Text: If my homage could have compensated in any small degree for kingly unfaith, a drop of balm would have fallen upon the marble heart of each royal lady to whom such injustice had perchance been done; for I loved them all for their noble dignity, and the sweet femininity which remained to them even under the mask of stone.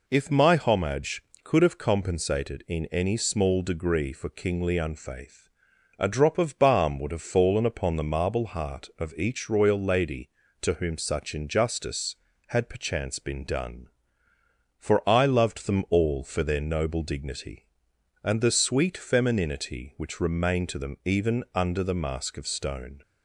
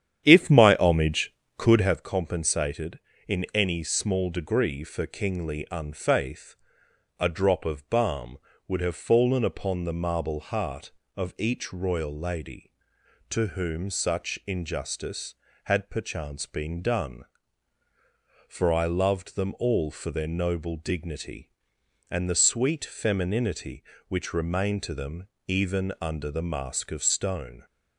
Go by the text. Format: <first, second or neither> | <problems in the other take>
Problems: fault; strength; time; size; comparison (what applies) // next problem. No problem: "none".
first | starts louder than the rest; strong; until 2.0 s; 9.5 dB // pauses between "them" and "even"; slight; at 25.2 s; 0.18 s long